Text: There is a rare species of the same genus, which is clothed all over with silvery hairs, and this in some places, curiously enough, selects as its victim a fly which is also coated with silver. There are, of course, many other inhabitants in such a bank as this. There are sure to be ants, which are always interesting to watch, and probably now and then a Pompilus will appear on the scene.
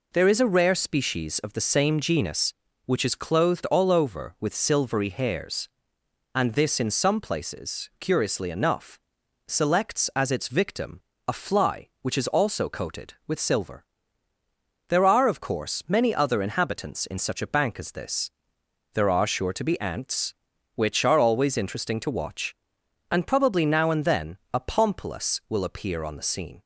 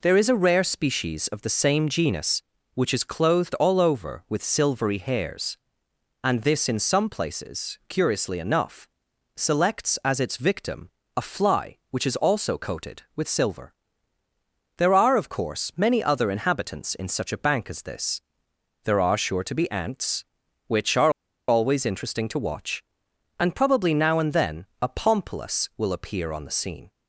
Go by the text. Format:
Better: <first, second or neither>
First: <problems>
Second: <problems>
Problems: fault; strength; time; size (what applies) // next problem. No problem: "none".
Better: first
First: pauses between "victim" and "a"; slight; at 10.9 s; 0.28 s long // pauses between "then" and "a"; slight; at 24.3 s; 0.16 s long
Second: pauses between "victim" and "a"; slight; at 10.8 s; 0.28 s long // pauses between "are" and "always"; at 21.1 s; 0.38 s long // pauses between "then" and "a"; slight; at 24.6 s; 0.16 s long